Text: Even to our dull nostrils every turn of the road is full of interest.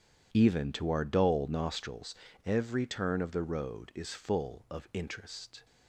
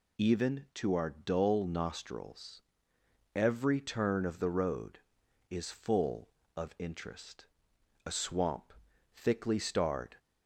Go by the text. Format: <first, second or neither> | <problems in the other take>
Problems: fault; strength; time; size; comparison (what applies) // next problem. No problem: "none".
first | pauses between "nostrils" and "every"; noticeable; at 2.6 s; 0.74 s long; slight in the first // goes on to say "A swamp thickly starred"; strong; from 8.0 s on; 2.1 s long